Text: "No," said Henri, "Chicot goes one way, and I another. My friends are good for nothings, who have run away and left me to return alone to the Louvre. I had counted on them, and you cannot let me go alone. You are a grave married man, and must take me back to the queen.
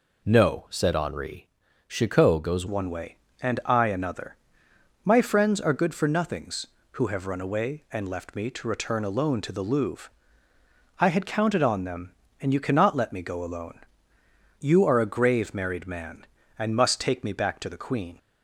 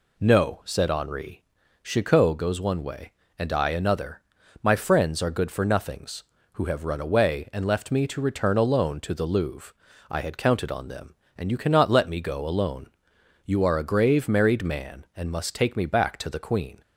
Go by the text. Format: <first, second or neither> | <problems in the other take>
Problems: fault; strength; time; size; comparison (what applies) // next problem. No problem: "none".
second | changes voice at "one"; from 2.6 s on; 15.5 s long